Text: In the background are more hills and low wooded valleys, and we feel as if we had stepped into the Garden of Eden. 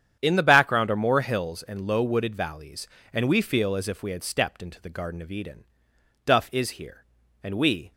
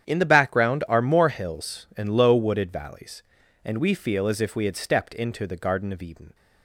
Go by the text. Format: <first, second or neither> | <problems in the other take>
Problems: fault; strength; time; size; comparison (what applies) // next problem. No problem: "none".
second | starts louder than the rest; strong; until 1.2 s; 9 dB; strong in the second // goes on to say "Duff is here and we"; from 6.2 s on; 1.6 s long